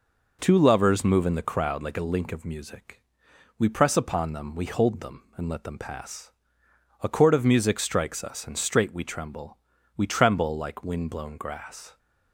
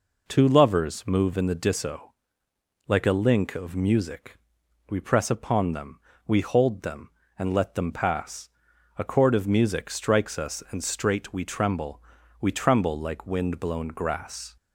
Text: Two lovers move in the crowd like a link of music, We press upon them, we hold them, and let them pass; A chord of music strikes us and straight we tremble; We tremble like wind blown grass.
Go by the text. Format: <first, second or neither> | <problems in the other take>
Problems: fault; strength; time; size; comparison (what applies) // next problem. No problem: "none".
first | says "disso" for "crowd"; at 1.5 s